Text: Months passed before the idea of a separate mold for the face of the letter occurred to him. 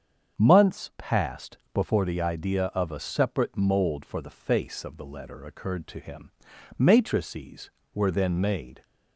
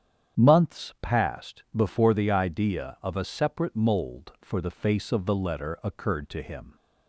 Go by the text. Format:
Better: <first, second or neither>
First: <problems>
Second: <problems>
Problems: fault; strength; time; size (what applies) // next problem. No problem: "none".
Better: second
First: starts louder than the rest; strong; until 1.4 s; 7.5 dB // pauses between "passed" and "before"; slight; at 1.5 s; 0.16 s long // goes on to say "Matrices were then made"; strong; from 6.7 s on; 2.0 s long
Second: starts louder than the rest; strong; until 1.4 s; 8.5 dB